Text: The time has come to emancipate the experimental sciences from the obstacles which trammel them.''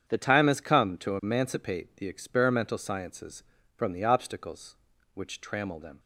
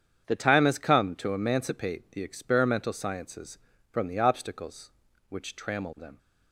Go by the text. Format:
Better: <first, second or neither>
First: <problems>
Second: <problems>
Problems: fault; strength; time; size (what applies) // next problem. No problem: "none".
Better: neither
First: starts louder than the rest; strong; until 1.1 s; 8 dB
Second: starts louder than the rest; strong; until 1.2 s; 8 dB